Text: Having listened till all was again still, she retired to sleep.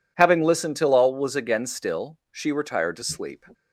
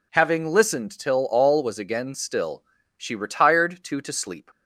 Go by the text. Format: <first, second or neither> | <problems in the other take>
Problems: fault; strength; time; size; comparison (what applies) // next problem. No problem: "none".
first | says "to" twice; at 3.9 s